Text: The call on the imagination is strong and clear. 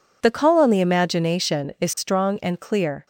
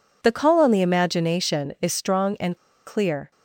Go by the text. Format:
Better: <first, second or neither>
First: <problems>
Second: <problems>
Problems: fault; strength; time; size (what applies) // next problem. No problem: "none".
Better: first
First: none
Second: pauses between "and" and "clear"; slight; at 2.5 s; 0.28 s long